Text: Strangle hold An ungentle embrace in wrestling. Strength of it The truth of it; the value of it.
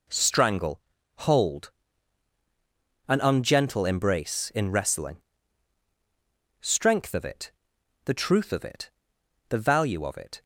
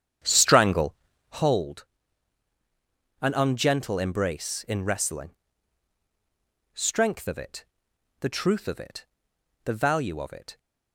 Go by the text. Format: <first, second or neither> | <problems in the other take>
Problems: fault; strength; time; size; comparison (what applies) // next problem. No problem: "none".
first | starts louder than the rest; strong; until 1.4 s; 9 dB // pauses between "Strangle" and "hold"; slight; at 0.9 s; 0.36 s long; slight in the first // pauses between "hold" and "An"; strong; at 1.8 s; 1.3 s long; strong in the first // pauses between "it" and "The"; noticeable; at 7.6 s; 0.56 s long; noticeable in the first